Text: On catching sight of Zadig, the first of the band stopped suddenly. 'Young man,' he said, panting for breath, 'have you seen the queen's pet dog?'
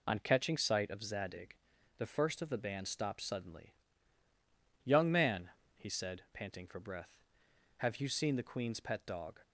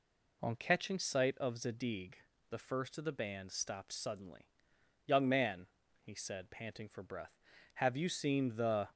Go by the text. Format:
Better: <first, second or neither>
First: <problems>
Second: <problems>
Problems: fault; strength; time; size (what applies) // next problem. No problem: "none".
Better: first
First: none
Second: stops before "queen's pet dog"; at 8.9 s